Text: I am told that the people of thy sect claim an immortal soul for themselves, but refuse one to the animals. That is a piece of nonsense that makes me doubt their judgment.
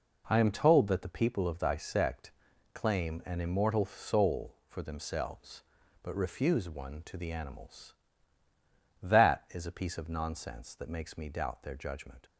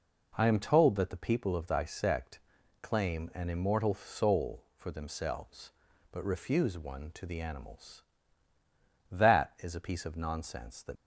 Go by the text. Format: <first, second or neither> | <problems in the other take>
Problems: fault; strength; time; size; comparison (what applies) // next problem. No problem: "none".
first | pauses between "sect" and "claim"; at 2.3 s; 0.42 s long; also in the first // stops before "makes me doubt their judgment"; at 10.9 s